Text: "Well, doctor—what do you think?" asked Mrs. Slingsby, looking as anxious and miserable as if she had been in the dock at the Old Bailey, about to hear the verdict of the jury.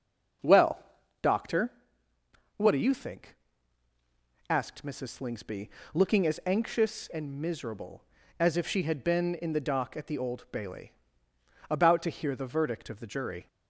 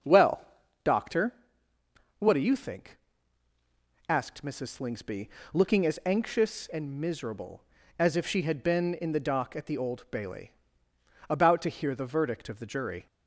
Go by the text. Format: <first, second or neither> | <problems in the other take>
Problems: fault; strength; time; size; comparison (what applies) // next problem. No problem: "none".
neither | starts louder than the rest; the same in both